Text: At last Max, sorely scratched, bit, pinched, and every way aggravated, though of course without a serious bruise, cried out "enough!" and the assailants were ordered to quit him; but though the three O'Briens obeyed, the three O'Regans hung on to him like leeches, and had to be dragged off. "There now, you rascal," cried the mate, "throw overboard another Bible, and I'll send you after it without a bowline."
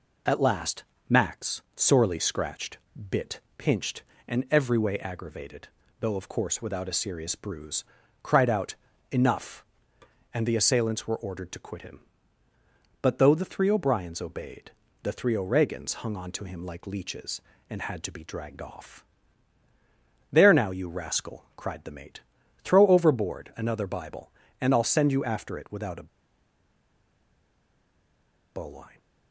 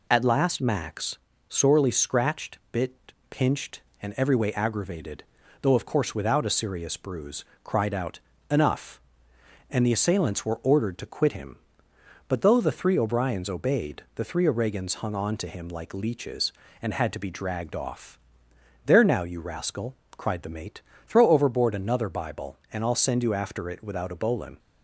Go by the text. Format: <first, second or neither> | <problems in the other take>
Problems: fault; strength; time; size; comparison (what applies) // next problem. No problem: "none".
second | pauses between "last" and "Max"; slight; at 0.8 s; 0.26 s long // pauses between "out" and "enough"; slight; at 8.7 s; 0.34 s long; slight in the second // pauses between "a" and "bowline"; strong; at 26.0 s; 2.4 s long